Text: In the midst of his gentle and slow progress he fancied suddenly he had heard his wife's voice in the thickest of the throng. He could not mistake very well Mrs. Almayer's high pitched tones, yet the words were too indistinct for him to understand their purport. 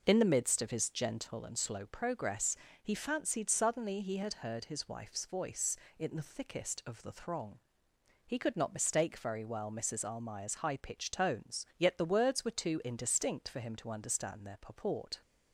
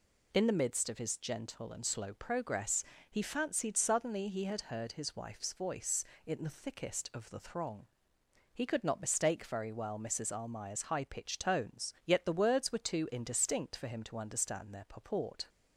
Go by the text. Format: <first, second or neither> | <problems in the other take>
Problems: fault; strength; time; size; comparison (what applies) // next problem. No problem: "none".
second | starts louder than the rest; noticeable; until 1.5 s; 5.5 dB // pauses between "progress" and "he"; slight; at 2.5 s; 0.24 s long; slight in the second